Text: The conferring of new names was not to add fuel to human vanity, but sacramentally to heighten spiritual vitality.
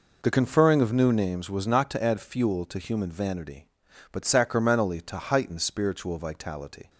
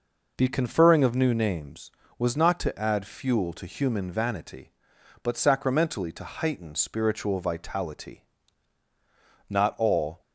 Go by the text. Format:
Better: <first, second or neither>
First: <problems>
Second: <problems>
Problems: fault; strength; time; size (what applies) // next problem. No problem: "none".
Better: first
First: none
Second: goes on to say "Not all"; noticeable; from 9.4 s on; 0.72 s long